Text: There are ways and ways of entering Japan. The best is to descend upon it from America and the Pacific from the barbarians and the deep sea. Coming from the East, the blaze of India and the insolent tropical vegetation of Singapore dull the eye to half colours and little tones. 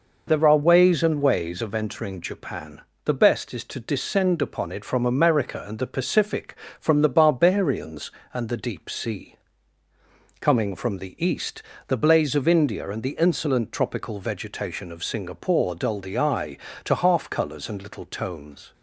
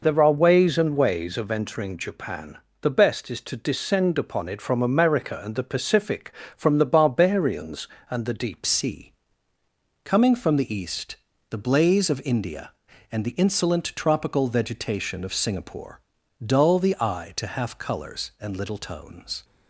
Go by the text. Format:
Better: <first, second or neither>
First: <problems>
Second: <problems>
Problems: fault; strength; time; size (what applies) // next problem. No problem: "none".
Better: first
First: none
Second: changes voice at "sea"; from 8.6 s on; 10.8 s long // pauses between "Singapore" and "dull"; at 16.0 s; 0.44 s long